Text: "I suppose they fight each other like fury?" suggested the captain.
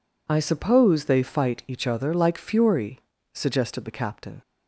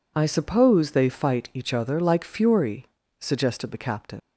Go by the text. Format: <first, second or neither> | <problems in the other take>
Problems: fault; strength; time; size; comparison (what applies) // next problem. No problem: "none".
first | leaves "captain" unfinished; at 4.1 s; 75 ms